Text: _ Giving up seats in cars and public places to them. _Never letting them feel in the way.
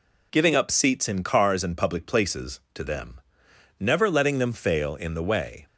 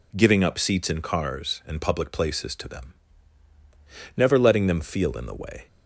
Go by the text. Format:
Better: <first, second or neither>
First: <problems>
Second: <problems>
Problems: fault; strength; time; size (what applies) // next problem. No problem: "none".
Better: second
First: says "fail" for "feel"; at 4.5 s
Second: none